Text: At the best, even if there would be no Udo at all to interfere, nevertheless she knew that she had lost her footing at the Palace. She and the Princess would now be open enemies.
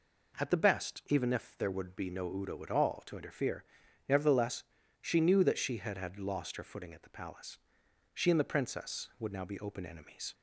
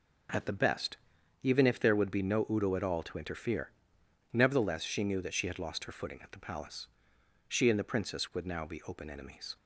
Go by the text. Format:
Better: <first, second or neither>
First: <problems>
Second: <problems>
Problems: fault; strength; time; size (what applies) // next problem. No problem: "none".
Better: second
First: pauses between "nevertheless" and "she"; slight; at 4.6 s; 0.36 s long // says "had" twice; at 5.9 s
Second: none